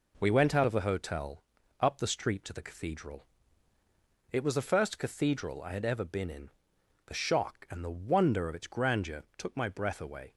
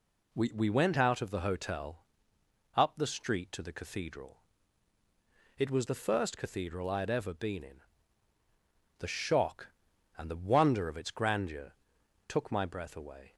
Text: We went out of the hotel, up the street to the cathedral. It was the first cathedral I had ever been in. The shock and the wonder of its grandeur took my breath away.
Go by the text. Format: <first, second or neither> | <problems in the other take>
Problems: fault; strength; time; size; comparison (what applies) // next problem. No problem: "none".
first | says "We" twice; at 0.5 s // pauses between "grandeur" and "took"; noticeable; at 11.7 s; 0.56 s long